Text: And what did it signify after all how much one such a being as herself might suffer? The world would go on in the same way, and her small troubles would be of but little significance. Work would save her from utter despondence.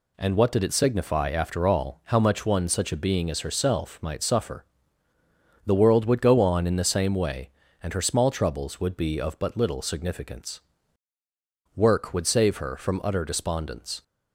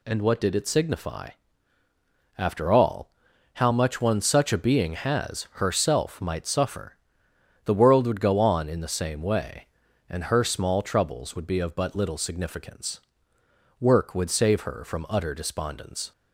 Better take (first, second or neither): first